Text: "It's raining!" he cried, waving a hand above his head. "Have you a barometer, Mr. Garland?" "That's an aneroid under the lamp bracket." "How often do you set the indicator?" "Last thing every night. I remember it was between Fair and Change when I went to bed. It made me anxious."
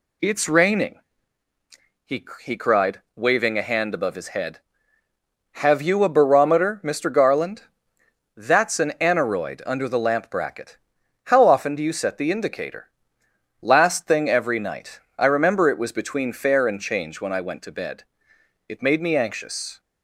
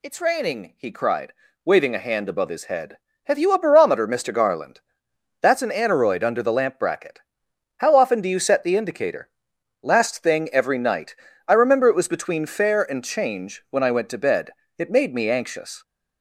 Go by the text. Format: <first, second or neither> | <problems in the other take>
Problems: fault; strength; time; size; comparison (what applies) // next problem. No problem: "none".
second | says "he" twice; at 2.4 s